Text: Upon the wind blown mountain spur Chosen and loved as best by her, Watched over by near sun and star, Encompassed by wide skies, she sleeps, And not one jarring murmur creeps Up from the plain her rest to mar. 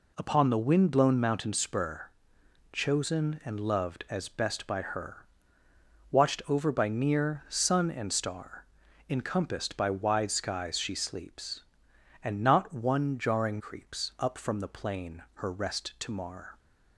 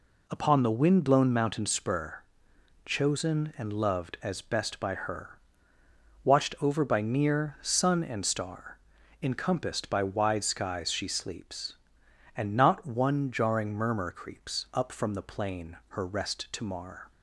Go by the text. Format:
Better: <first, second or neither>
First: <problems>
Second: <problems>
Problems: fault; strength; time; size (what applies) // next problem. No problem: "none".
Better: second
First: pauses between "spur" and "Chosen"; noticeable; at 2.0 s; 0.64 s long // skips "murmur"; at 13.5 s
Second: pauses between "spur" and "Chosen"; noticeable; at 2.2 s; 0.64 s long